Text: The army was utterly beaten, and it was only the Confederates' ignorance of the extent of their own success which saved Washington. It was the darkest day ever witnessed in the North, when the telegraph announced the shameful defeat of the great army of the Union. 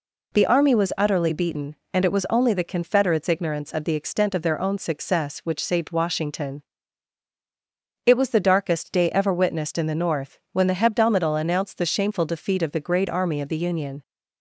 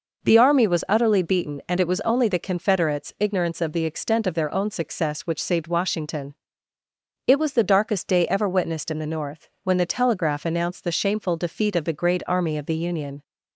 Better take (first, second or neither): second